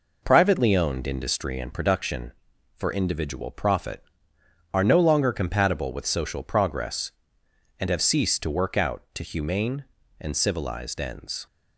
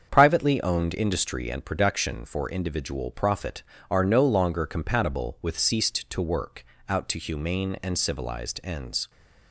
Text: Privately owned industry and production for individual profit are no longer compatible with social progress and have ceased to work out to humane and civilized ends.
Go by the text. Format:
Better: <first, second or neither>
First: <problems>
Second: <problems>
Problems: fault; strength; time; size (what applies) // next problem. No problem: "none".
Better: first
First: none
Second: starts louder than the rest; strong; until 1.1 s; 7 dB // skips "social progress and have"; at 5.5 s // pauses between "work" and "out"; slight; at 6.6 s; 0.24 s long